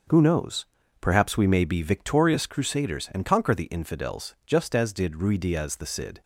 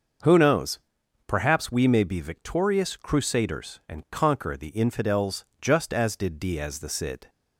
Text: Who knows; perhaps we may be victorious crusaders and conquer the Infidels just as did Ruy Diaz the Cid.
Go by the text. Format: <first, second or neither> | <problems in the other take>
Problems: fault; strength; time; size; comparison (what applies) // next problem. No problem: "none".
first | starts louder than the rest; until 1.7 s; 6.5 dB; also in the first // pauses between "Infidels" and "just"; slight; at 5.4 s; 0.16 s long // skips "Ruy"; at 6.4 s